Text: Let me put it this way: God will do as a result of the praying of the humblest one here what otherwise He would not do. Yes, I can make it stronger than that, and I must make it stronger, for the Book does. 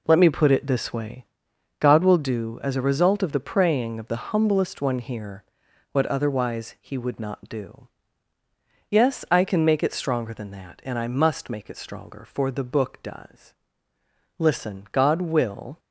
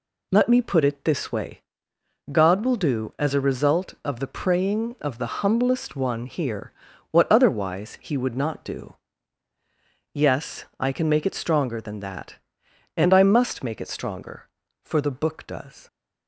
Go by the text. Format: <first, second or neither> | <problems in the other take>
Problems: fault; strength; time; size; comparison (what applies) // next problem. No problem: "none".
second | pauses between "here" and "what"; noticeable; at 5.4 s; 0.50 s long; also in the second // goes on to say "Listen God will"; from 14.3 s on; 1.4 s long